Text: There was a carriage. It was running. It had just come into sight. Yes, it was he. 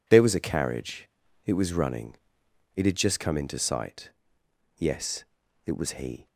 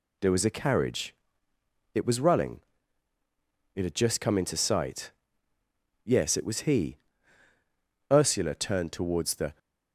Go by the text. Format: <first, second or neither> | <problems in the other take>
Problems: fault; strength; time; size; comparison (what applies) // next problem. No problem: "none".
first | goes on to say "Ursula turned towards the"; from 8.1 s on; 1.4 s long